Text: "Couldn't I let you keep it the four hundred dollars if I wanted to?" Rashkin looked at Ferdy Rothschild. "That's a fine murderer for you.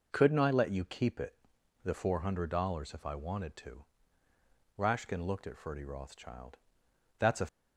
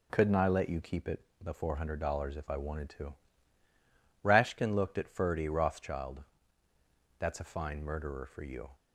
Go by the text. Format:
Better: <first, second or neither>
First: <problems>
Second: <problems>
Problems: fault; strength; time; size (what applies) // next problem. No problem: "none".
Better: second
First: pauses between "it" and "the"; noticeable; at 1.3 s; 0.48 s long // stops before "fine murderer for you"; at 7.4 s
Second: pauses between "it" and "the"; slight; at 1.2 s; 0.16 s long